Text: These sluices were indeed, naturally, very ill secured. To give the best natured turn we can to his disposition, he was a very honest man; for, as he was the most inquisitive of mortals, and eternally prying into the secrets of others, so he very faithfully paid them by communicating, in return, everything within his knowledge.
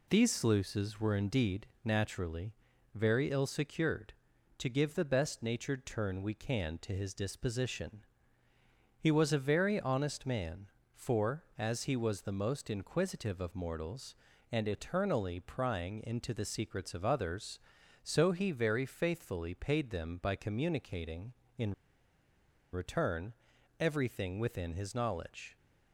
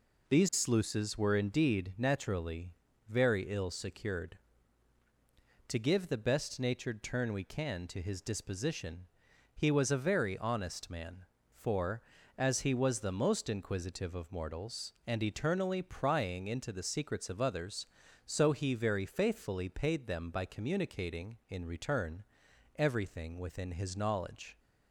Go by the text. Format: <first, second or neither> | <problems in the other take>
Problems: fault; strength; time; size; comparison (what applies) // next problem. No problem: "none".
second | pauses between "in" and "return"; at 21.7 s; 0.98 s long